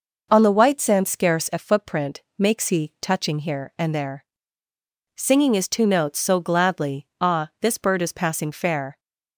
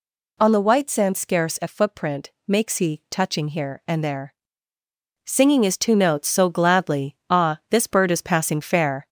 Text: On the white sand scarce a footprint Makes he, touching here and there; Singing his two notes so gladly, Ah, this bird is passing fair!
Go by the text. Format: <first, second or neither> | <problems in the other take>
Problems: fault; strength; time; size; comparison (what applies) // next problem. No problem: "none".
first | gets louder; slight; throughout; 2 dB // pauses between "footprint" and "Makes"; slight; at 2.3 s; 0.16 s long; slight in the first